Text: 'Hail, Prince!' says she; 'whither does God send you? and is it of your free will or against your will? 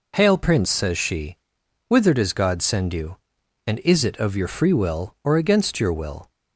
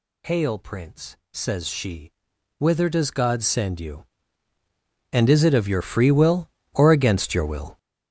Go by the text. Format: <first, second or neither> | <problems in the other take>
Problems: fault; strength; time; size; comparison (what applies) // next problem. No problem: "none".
first | gets louder; strong; throughout; 9.5 dB